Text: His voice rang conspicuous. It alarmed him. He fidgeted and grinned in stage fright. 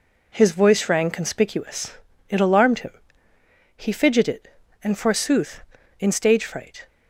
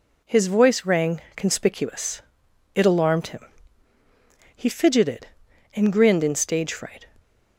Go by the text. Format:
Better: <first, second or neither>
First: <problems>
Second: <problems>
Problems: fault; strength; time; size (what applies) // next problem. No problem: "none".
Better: second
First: says "forsooth" for "grinned"; at 4.9 s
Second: none